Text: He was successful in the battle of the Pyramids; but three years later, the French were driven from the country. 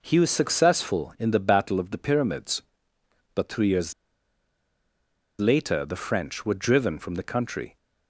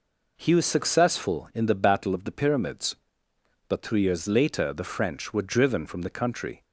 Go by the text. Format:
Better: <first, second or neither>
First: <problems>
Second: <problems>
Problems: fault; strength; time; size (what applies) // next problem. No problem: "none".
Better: second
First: pauses between "years" and "later"; strong; at 3.9 s; 1.4 s long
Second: none